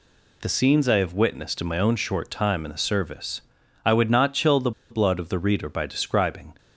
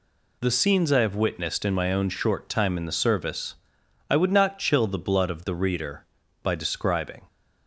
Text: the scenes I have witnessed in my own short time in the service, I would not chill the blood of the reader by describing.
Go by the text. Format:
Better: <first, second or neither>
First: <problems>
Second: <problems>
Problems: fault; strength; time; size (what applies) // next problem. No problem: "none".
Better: second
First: pauses between "the" and "blood"; slight; at 4.7 s; 0.20 s long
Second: none